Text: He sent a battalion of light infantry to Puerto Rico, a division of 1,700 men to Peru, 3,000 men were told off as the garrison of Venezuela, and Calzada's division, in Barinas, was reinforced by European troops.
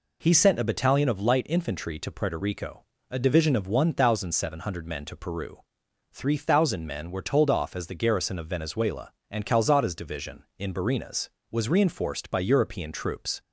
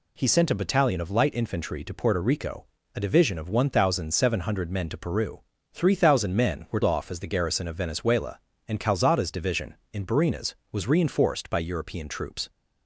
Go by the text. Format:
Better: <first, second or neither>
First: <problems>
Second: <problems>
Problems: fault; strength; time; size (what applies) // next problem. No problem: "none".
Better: first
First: none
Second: skips "told"; at 6.8 s